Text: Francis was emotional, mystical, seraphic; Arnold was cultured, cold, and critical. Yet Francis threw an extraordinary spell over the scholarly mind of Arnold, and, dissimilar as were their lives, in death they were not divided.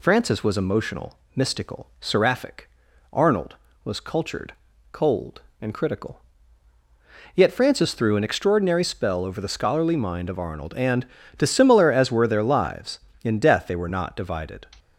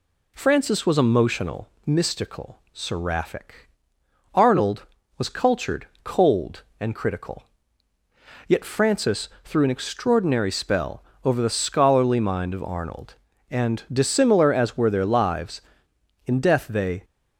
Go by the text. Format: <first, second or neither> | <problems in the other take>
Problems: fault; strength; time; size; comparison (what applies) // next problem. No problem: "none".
first | pauses between "Francis" and "threw"; slight; at 9.2 s; 0.16 s long // pauses between "spell" and "over"; slight; at 11.0 s; 0.20 s long // stops before "were not divided"; at 17.0 s